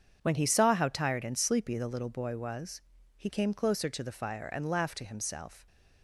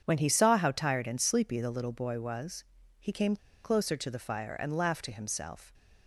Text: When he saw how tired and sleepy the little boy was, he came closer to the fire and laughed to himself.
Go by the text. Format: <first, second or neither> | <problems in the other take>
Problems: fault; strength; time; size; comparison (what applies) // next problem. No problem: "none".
first | starts louder than the rest; strong; until 1.0 s; 7.5 dB; strong in the first // pauses between "came" and "closer"; slight; at 3.3 s; 0.27 s long